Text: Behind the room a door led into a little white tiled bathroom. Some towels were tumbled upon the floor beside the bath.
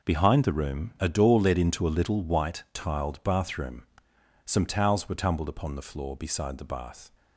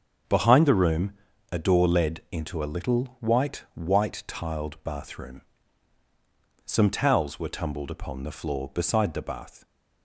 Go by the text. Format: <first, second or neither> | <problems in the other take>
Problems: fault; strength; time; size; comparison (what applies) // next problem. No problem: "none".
first | starts louder than the rest; until 1.6 s; 6 dB // pauses between "room" and "a"; at 1.1 s; 0.38 s long // says "white" twice; at 3.7 s